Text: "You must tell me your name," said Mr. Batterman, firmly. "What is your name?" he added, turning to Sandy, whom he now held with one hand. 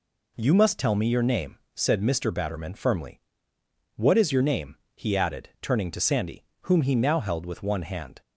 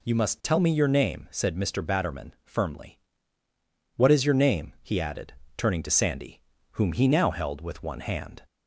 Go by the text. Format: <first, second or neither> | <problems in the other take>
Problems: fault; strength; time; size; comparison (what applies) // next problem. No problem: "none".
neither | none